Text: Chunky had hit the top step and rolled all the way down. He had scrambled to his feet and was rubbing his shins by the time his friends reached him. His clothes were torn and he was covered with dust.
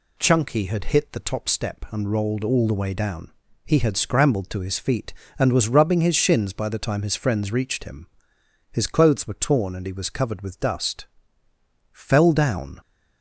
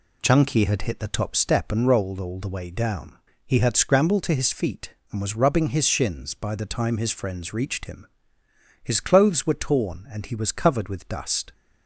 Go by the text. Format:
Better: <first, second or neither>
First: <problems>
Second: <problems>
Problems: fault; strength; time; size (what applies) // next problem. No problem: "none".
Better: second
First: goes on to say "Fell down"; noticeable; from 11.9 s on; 0.88 s long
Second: none